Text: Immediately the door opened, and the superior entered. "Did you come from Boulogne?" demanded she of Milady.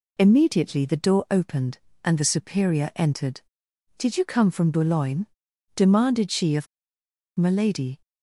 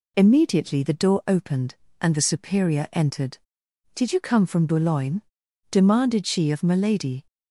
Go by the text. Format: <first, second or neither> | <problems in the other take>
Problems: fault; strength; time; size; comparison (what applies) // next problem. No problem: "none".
second | pauses between "of" and "Milady"; noticeable; at 6.6 s; 0.70 s long